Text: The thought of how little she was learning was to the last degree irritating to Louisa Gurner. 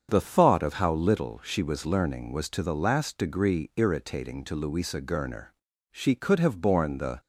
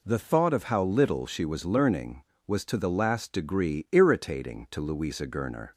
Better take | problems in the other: second | starts louder than the rest; strong; until 1.1 s; 7 dB // goes on to say "She could have borne the"; noticeable; from 5.9 s on; 1.2 s long

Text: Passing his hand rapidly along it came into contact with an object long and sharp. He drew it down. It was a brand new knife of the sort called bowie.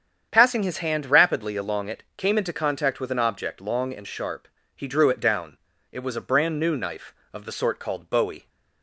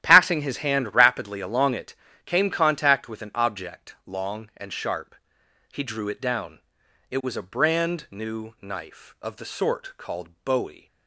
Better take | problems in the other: first | starts louder than the rest; strong; until 1.0 s; 11.5 dB; strong in the first // pauses between "it" and "came"; slight; at 1.9 s; 0.30 s long // skips "into"; at 2.5 s // pauses between "called" and "bowie"; slight; at 10.2 s; 0.16 s long

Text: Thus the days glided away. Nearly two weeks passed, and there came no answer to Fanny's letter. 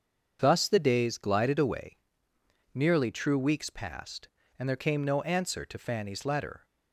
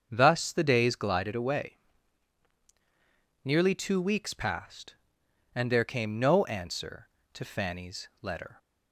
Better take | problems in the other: second | starts louder than the rest; until 1.4 s; 7 dB; also in the second // says "true" for "two"; at 3.1 s

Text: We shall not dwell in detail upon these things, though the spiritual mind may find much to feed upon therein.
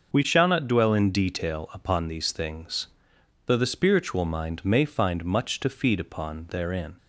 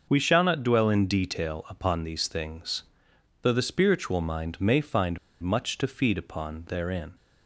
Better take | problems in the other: first | pauses between "find" and "much"; slight; at 5.1 s; 0.24 s long

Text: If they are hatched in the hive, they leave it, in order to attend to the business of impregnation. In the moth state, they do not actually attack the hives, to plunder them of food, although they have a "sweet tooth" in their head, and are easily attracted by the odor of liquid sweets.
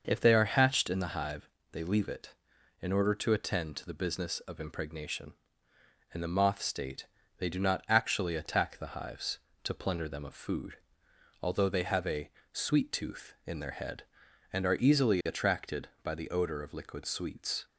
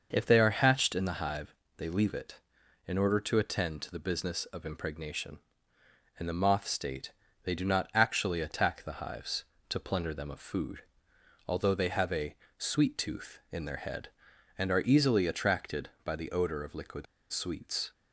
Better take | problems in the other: first | starts louder than the rest; until 1.1 s; 6 dB; also in the first // pauses between "a" and "sweet"; slight; at 12.3 s; 0.22 s long; slight in the first // pauses between "liquid" and "sweets"; slight; at 17.0 s; 0.26 s long

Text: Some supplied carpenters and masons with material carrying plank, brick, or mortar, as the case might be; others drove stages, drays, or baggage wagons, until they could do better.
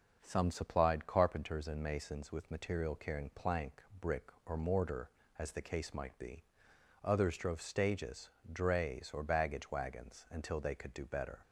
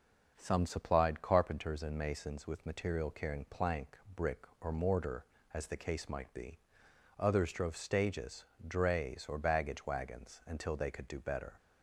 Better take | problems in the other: neither | none

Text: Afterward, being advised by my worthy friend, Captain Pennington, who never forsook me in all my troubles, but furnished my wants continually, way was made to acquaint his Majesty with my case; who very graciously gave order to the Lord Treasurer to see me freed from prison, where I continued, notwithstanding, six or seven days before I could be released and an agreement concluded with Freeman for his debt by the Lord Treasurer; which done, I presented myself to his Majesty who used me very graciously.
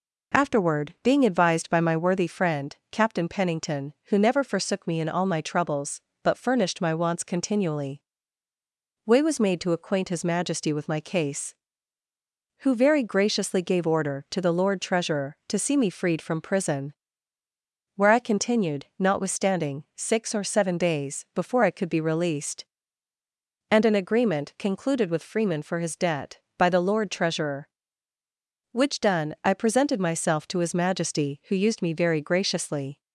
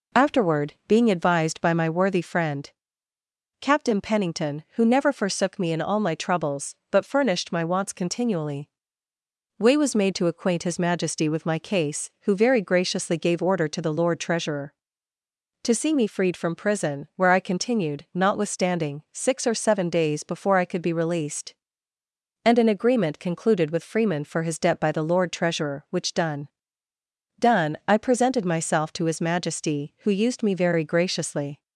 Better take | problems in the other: first | says "done" twice; at 27.3 s

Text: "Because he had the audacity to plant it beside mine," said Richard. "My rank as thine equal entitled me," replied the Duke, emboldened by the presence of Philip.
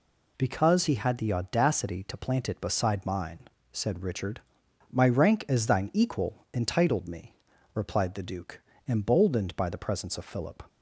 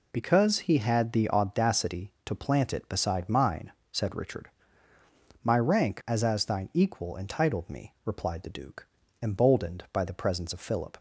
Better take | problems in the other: first | says "as" twice; at 6.2 s

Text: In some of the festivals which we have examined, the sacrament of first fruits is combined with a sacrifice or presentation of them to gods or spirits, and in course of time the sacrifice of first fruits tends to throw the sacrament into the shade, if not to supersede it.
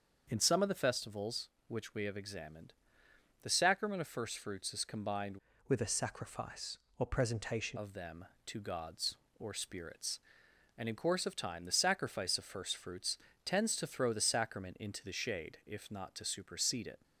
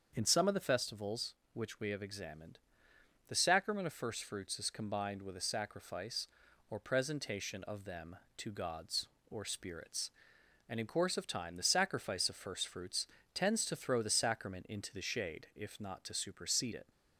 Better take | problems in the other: second | starts louder than the rest; until 1.3 s; 6.5 dB; also in the second // changes voice from "with" to "presentation"; from 5.6 to 7.7 s; 2.1 s long // pauses between "fruits" and "tends"; slight; at 13.1 s; 0.28 s long; slight in the second

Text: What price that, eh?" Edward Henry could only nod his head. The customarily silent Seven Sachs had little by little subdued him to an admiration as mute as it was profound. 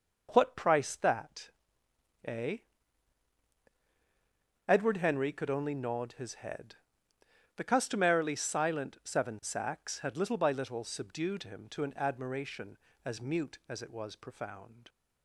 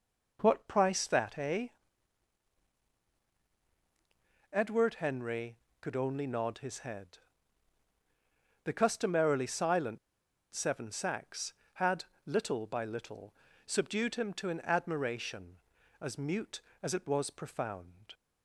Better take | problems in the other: first | pauses between "silent" and "Seven"; noticeable; at 9.9 s; 0.55 s long // pauses between "had" and "little"; slight; at 12.0 s; 0.22 s long // pauses between "little" and "subdued"; slight; at 13.3 s; 0.32 s long

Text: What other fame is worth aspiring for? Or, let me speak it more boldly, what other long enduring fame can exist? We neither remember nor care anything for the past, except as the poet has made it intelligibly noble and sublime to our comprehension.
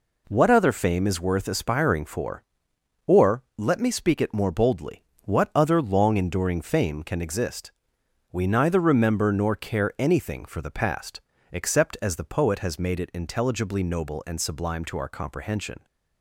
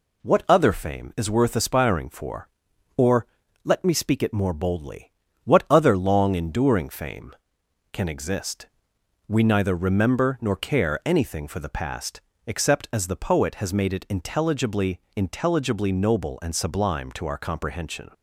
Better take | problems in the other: first | says "intelligibly" twice; at 15.1 s

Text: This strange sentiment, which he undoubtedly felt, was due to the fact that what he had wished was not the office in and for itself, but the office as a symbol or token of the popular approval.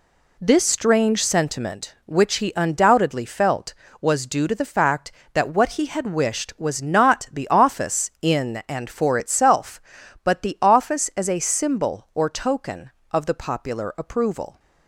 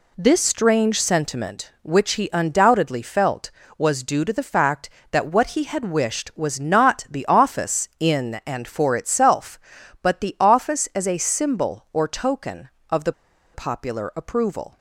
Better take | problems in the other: first | pauses between "the" and "popular"; at 13.1 s; 0.42 s long

